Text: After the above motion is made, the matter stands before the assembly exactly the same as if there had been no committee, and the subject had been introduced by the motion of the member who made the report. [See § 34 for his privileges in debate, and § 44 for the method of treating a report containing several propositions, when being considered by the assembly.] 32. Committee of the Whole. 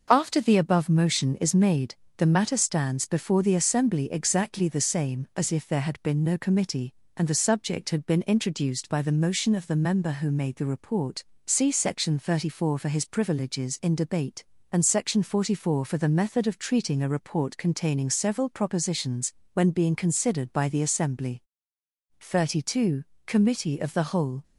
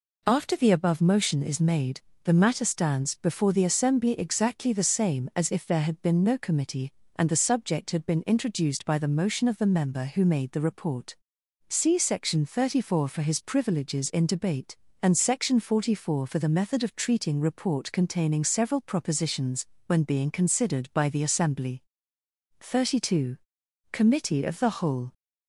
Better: first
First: none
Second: skips "a"; at 17.4 s

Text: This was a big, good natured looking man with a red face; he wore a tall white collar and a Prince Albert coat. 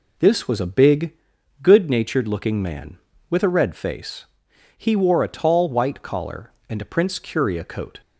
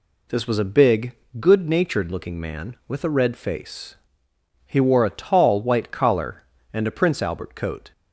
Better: second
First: says "Curia" for "Albert"; at 7.1 s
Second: none

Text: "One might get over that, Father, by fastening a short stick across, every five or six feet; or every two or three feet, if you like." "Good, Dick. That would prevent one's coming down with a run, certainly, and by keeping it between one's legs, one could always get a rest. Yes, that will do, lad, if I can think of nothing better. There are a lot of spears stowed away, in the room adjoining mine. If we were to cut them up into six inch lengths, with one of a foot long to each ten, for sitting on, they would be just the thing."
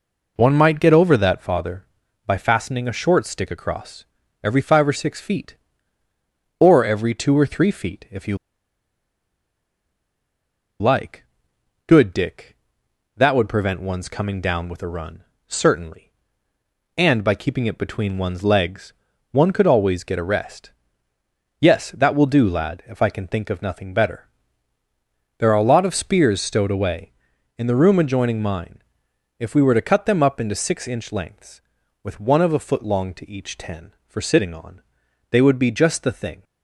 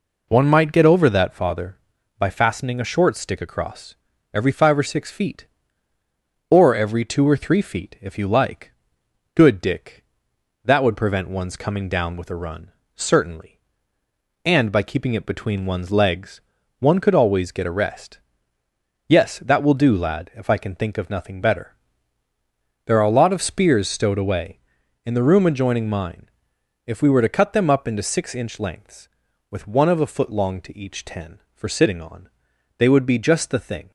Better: second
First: pauses between "you" and "like"; strong; at 8.3 s; 2.4 s long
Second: none

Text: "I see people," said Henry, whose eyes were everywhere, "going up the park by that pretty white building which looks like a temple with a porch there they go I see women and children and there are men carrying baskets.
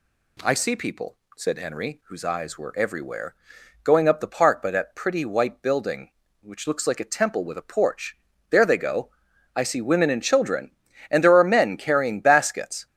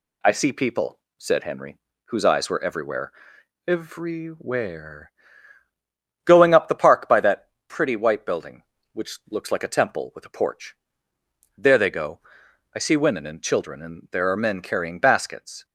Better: first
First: pauses between "porch" and "there"; slight; at 8.1 s; 0.34 s long // pauses between "go" and "I"; noticeable; at 9.1 s; 0.46 s long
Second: says "everywhere" twice; at 3.6 s // pauses between "that" and "pretty"; slight; at 7.4 s; 0.18 s long // pauses between "porch" and "there"; noticeable; at 10.7 s; 0.82 s long // pauses between "go" and "I"; noticeable; at 12.1 s; 0.56 s long

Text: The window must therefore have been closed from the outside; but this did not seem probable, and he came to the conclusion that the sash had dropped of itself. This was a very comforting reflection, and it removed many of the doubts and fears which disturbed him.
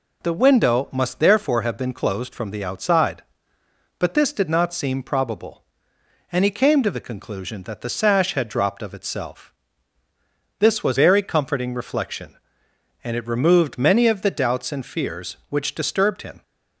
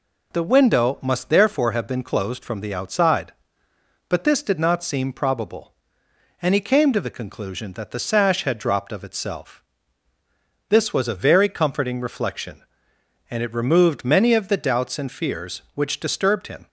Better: second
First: skips "a"; at 10.9 s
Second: none

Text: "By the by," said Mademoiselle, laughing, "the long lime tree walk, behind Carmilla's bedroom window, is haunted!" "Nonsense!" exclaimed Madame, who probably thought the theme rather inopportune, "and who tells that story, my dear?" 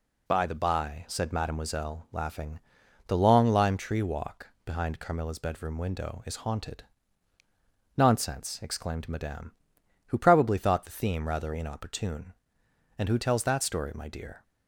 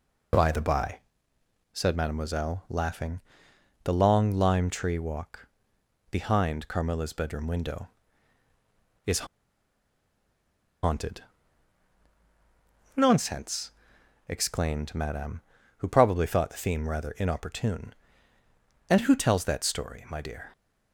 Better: first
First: none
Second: pauses between "is" and "haunted"; strong; at 9.2 s; 1.5 s long

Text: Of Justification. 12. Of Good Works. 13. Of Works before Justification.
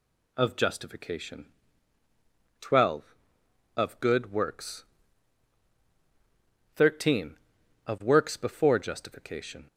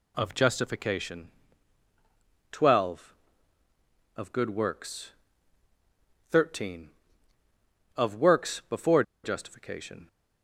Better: first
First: none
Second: pauses between "before" and "Justification"; slight; at 9.0 s; 0.21 s long

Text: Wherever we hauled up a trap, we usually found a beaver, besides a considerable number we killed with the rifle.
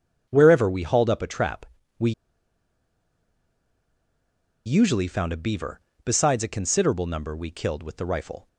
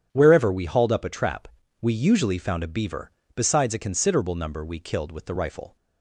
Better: second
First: starts louder than the rest; strong; until 1.3 s; 9 dB // pauses between "we" and "usually"; strong; at 2.1 s; 2.5 s long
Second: starts louder than the rest; strong; until 1.1 s; 9 dB

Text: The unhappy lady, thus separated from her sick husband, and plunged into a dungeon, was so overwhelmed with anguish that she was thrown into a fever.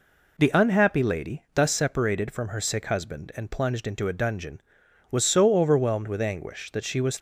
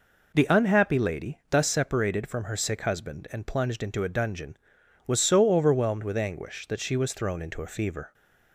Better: second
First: stops before "thrown into a fever"; at 7.1 s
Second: none

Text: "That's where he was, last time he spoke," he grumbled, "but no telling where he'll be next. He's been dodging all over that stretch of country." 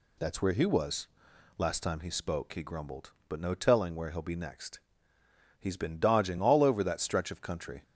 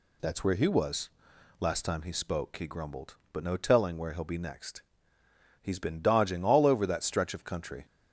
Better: neither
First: none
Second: none

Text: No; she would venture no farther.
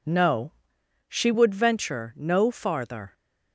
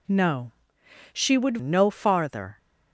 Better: first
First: none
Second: skips "venture"; at 1.5 s

